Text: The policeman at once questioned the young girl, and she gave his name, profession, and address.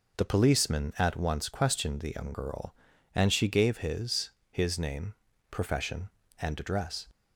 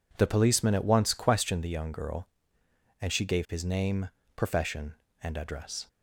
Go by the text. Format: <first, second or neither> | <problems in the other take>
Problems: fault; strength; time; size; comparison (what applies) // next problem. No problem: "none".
second | says "his" twice; at 4.5 s